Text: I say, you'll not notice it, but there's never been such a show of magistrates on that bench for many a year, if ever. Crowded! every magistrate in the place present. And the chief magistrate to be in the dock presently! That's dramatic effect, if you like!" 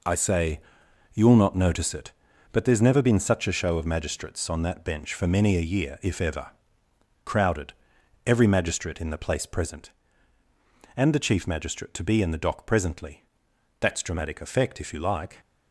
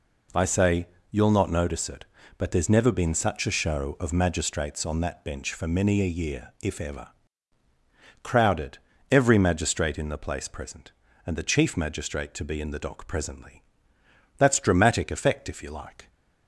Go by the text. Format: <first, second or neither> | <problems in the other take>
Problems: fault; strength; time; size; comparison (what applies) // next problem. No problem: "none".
neither | none